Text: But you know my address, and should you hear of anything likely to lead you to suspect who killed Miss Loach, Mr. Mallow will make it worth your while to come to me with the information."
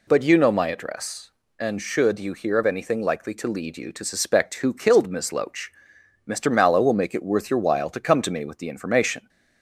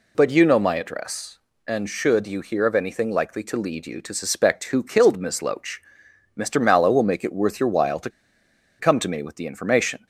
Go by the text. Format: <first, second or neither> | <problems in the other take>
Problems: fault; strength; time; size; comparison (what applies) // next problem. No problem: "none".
first | pauses between "to" and "come"; noticeable; at 8.0 s; 0.71 s long